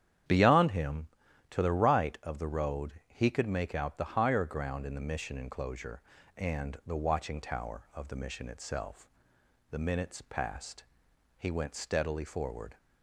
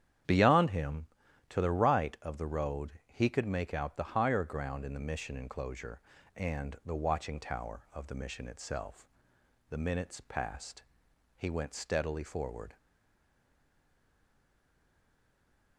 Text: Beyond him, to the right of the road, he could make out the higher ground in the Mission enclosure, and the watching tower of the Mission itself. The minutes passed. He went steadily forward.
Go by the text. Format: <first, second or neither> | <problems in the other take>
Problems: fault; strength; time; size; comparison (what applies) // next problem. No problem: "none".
first | starts louder than the rest; strong; until 1.6 s; 9.5 dB; strong in the first // stays silent after the last word; strong; from 12.7 s on; 3.0 s long